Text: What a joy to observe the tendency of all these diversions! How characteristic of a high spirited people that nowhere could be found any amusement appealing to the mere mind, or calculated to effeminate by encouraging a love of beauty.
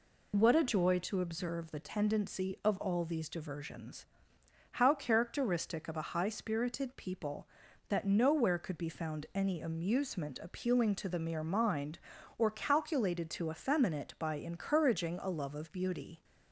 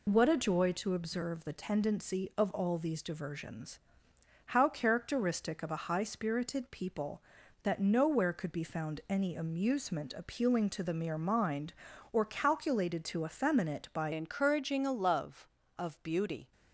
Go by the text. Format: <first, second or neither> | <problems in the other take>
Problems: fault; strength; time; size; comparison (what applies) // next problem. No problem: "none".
first | changes voice at "encouraging"; from 14.1 s on; 2.4 s long